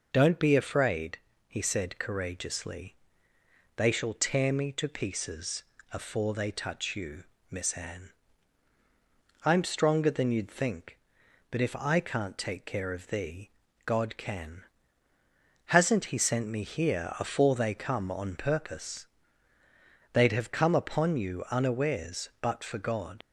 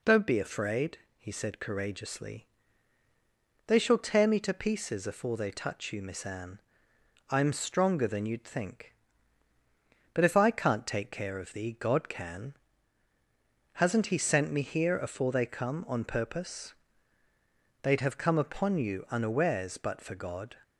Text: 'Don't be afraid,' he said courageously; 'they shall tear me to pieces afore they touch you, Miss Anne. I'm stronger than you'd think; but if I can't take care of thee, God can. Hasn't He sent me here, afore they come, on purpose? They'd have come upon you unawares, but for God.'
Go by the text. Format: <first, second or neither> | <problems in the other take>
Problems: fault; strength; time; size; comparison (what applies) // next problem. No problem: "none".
second | pauses between "pieces" and "afore"; slight; at 5.6 s; 0.28 s long // leaves "God" unfinished; at 23.2 s; 65 ms